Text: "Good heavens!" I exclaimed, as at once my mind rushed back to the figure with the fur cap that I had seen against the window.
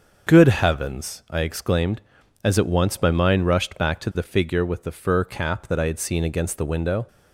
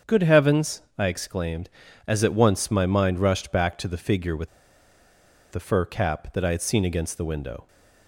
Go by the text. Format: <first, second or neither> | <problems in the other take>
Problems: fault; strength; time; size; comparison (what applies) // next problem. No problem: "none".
first | starts louder than the rest; strong; until 1.2 s; 7.5 dB; also in the first // pauses between "with" and "the"; at 4.4 s; 1.0 s long